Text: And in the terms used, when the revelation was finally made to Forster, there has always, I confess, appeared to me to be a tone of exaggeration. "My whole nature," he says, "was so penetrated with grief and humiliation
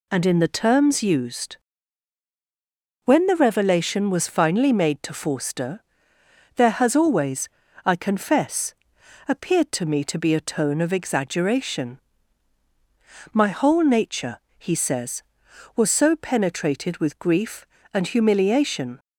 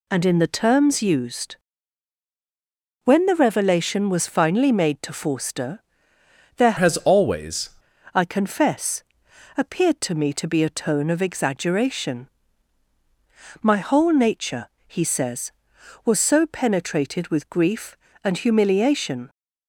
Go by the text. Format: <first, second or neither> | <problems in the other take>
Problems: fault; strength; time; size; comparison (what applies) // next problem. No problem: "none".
first | changes voice from "has" to "always"; from 6.7 to 7.6 s; 0.9 s long